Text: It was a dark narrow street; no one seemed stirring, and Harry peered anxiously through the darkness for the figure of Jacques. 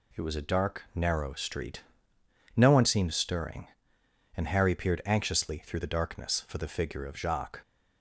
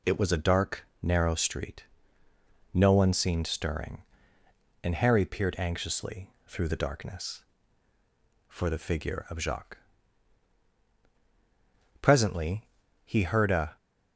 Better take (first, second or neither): first